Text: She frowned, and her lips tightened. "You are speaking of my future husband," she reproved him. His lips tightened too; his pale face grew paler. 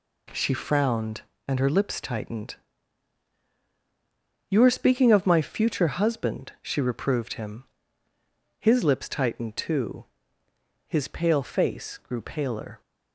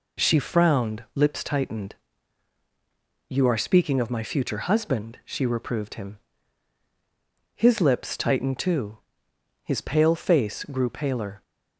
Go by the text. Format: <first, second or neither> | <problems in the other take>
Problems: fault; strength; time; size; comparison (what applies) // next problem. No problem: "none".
first | skips "and her"; at 1.0 s